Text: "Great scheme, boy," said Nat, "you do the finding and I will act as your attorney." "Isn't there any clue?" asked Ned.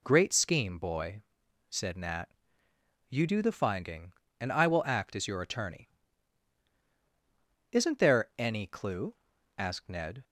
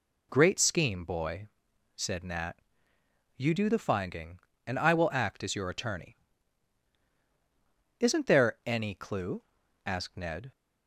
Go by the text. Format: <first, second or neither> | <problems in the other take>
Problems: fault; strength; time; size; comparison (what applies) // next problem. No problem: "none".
neither | none